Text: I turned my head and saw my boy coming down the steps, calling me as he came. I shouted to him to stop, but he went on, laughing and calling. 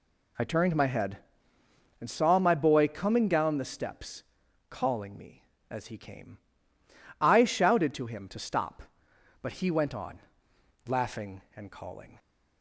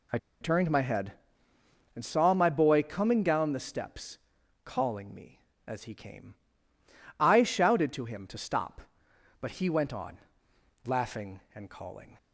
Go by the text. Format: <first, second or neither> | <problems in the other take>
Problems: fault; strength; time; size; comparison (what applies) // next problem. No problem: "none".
first | pauses between "I" and "turned"; slight; at 0.1 s; 0.23 s long